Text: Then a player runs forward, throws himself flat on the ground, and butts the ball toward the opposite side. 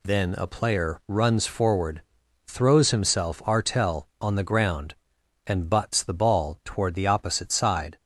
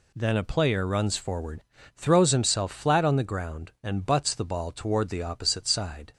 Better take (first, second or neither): second